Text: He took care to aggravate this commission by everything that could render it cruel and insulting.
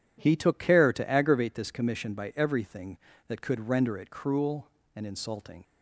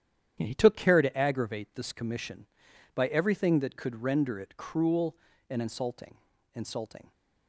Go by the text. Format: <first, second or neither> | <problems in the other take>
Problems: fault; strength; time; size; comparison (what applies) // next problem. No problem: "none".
first | starts louder than the rest; strong; until 1.4 s; 10 dB // says "insulting" twice; at 6.5 s